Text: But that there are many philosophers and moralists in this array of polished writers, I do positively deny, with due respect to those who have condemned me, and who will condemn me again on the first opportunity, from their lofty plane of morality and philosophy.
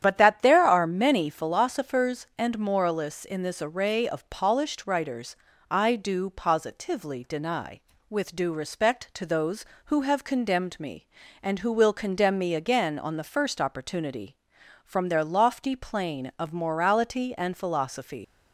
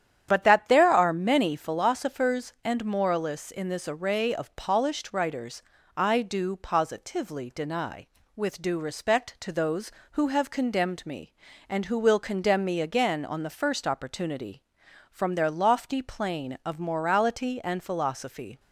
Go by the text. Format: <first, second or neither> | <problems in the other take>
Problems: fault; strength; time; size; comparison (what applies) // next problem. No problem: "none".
second | starts louder than the rest; strong; until 1.0 s; 10 dB; strong in the second // leaves "philosophy" unfinished; at 18.2 s; 85 ms